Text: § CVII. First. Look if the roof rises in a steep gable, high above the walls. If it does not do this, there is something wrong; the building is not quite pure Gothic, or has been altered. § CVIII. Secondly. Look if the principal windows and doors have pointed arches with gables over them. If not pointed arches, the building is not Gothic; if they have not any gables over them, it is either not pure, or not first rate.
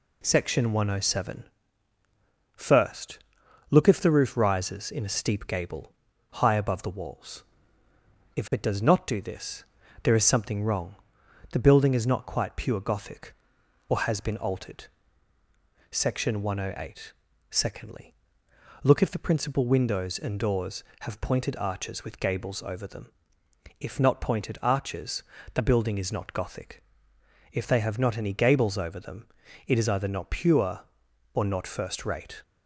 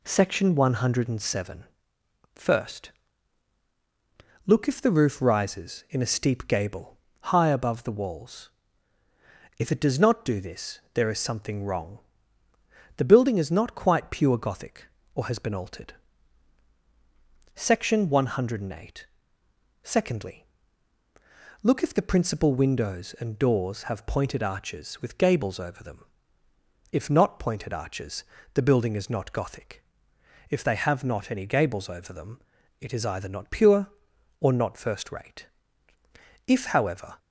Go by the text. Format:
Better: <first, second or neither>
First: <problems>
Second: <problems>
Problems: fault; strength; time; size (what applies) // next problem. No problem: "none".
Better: first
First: none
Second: goes on to say "If however"; noticeable; from 36.4 s on; 0.70 s long